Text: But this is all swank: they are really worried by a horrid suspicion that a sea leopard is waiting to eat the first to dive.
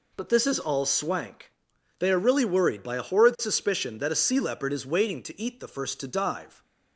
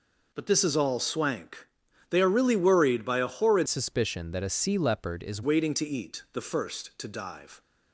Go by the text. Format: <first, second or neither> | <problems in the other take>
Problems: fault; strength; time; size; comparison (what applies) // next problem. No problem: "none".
first | changes voice from "suspicion" to "is"; from 3.6 to 5.4 s; 1.8 s long